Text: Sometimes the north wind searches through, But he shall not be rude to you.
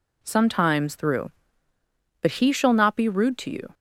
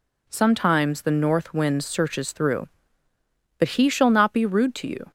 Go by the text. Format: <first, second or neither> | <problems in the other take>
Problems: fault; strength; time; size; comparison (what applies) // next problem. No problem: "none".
second | skips "the north wind searches"; at 0.9 s